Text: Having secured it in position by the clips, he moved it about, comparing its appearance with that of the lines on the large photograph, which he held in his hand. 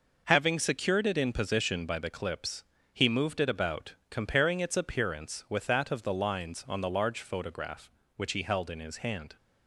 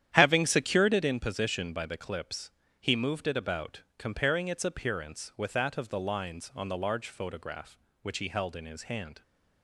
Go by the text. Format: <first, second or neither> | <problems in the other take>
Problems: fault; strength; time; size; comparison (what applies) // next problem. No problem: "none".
first | starts louder than the rest; strong; until 1.2 s; 10.5 dB